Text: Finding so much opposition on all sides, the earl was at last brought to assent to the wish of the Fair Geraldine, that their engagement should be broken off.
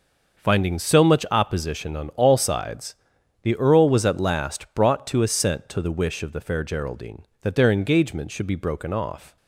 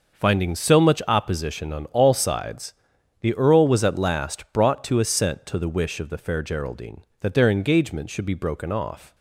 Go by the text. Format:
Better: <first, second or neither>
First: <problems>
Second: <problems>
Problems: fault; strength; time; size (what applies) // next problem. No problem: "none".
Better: neither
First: none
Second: none